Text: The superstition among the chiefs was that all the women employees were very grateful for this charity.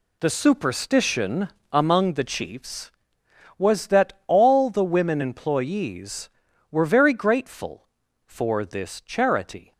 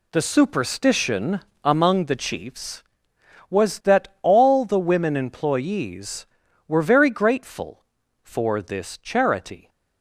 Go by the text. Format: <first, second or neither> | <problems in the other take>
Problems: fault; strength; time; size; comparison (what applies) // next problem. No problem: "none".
neither | pauses between "superstition" and "among"; slight; the same in both